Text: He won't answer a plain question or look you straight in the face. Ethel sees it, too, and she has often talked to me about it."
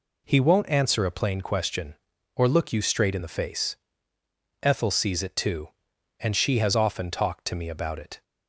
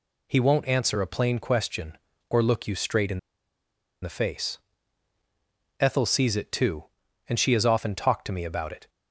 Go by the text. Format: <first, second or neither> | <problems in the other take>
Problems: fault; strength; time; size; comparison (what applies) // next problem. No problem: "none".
first | pauses between "in" and "the"; noticeable; at 3.1 s; 0.83 s long